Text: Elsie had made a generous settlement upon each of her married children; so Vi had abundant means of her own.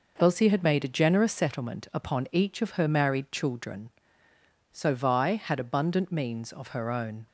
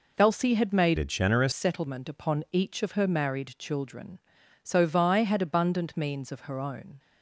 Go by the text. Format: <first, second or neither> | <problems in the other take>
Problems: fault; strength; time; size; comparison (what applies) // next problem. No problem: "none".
first | changes voice from "a" to "generous"; from 0.9 to 1.5 s; 0.6 s long